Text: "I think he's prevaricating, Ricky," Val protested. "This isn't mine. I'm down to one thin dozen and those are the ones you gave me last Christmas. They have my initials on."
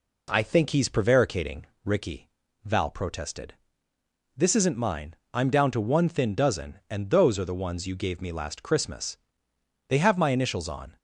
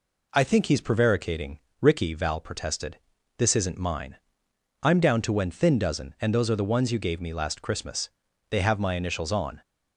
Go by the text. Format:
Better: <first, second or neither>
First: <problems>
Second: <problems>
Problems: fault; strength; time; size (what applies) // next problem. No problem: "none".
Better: first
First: none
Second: says "when" for "one"; at 5.3 s